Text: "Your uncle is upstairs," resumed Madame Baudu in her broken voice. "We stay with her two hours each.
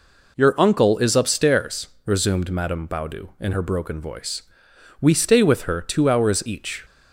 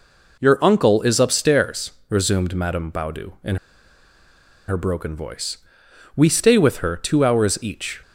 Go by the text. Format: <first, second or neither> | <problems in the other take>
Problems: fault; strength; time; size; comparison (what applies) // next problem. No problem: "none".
first | pauses between "in" and "her"; at 3.5 s; 1.1 s long